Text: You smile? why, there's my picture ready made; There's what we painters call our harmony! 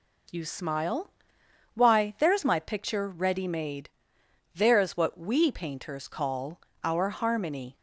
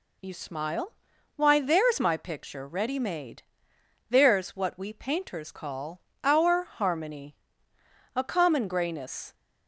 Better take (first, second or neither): first